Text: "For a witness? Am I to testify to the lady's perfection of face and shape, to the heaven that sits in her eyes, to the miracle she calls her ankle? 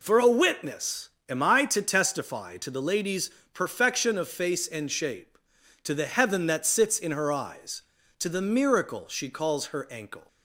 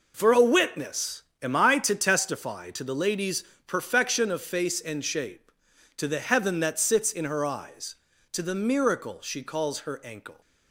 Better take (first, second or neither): first